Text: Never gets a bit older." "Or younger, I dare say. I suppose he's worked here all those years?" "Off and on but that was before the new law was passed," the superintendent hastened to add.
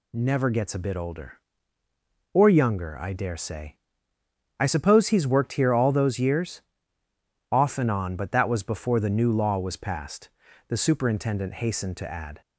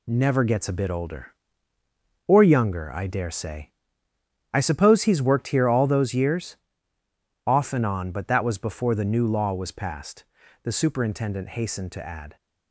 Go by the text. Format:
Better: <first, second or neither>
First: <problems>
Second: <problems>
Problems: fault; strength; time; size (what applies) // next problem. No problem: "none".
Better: first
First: none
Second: gets quieter; noticeable; throughout; 6 dB